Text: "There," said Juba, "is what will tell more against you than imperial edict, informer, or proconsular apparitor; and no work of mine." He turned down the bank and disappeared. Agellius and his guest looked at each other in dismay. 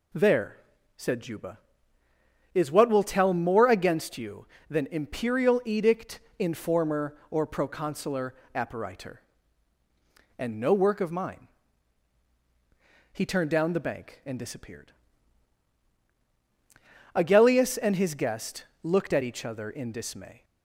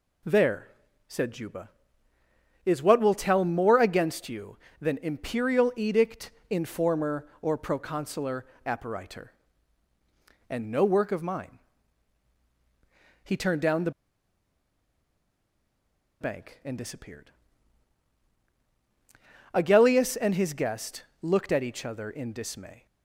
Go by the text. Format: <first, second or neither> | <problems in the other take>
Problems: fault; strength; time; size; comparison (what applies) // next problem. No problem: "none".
first | pauses between "proconsular" and "apparitor"; slight; at 8.4 s; 0.20 s long; slight in the first // pauses between "the" and "bank"; strong; at 13.8 s; 2.3 s long // pauses between "guest" and "looked"; slight; at 21.0 s; 0.18 s long; slight in the first